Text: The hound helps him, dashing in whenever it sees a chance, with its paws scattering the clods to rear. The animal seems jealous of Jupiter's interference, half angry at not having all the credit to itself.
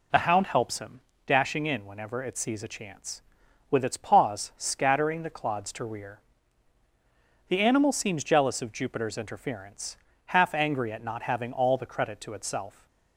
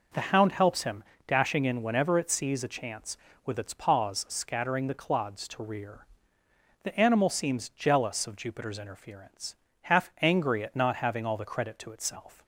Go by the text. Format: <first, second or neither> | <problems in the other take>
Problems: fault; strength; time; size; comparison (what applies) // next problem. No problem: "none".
neither | none